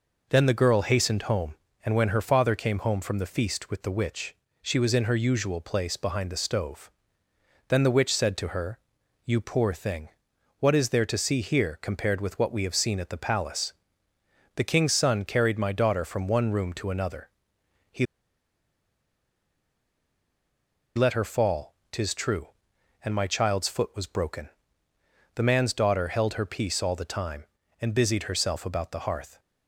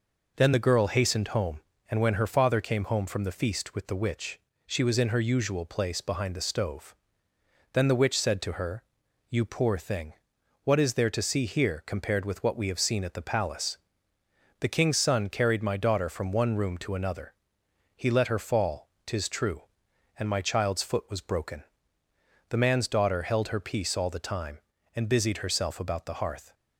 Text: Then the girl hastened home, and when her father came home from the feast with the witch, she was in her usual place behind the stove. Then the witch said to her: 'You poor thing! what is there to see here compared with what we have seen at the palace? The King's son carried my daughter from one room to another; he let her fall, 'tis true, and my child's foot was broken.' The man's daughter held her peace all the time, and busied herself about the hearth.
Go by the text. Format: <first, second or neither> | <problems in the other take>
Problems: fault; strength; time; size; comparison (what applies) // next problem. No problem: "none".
second | pauses between "he" and "let"; strong; at 18.0 s; 2.9 s long